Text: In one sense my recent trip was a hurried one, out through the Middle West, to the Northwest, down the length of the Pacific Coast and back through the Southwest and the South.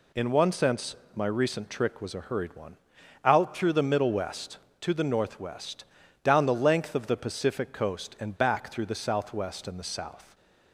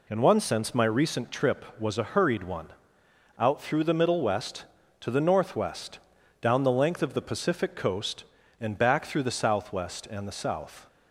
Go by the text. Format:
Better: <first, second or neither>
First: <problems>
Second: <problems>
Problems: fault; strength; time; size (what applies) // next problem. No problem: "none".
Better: second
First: pauses between "sense" and "my"; slight; at 0.9 s; 0.18 s long // says "trick" for "trip"; at 1.6 s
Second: none